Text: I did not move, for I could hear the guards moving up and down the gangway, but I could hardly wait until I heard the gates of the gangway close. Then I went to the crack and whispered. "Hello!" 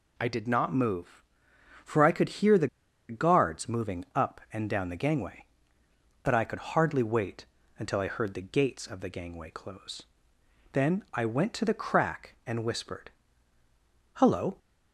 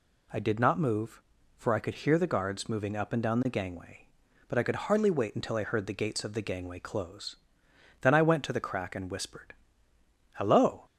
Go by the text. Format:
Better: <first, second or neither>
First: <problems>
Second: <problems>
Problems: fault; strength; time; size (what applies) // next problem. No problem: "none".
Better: second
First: pauses between "the" and "guards"; at 2.6 s; 0.42 s long // pauses between "wait" and "until"; slight; at 7.4 s; 0.34 s long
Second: none